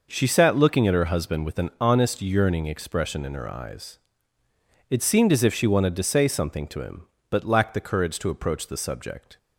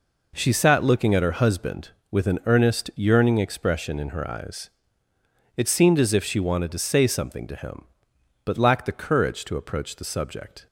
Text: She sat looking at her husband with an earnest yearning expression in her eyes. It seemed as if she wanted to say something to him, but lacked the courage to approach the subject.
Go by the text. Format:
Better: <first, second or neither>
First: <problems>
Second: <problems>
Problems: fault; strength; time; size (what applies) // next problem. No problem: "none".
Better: second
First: says "honest" for "earnest"; at 1.7 s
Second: none